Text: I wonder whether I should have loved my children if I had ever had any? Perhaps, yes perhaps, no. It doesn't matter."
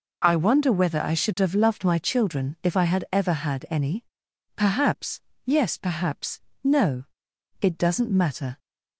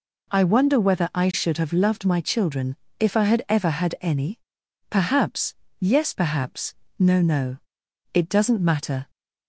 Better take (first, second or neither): first